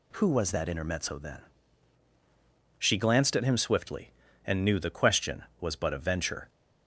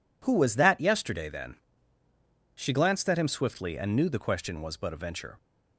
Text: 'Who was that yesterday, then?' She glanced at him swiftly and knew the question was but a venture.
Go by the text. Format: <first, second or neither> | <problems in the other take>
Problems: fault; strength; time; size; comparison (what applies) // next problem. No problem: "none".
second | says "intermezzo" for "yesterday"; at 0.6 s